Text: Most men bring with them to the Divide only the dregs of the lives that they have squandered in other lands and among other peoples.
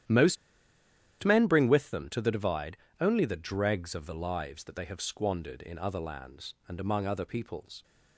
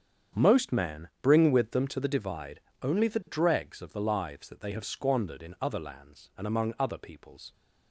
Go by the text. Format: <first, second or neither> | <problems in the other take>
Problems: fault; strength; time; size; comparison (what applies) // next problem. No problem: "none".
second | starts louder than the rest; strong; until 1.9 s; 11 dB; strong in the second // pauses between "Most" and "men"; noticeable; at 0.3 s; 0.86 s long // pauses between "Divide" and "only"; slight; at 2.7 s; 0.24 s long; slight in the second